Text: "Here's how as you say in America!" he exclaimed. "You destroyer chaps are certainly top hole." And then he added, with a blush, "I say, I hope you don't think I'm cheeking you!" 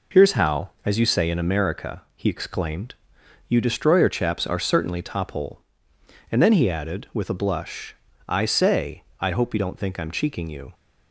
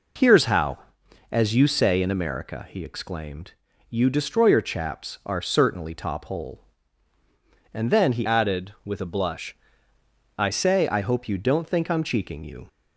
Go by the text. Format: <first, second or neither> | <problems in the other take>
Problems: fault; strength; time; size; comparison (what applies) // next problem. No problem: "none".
first | changes voice from "added" to "I"; from 8.2 to 10.4 s; 2.2 s long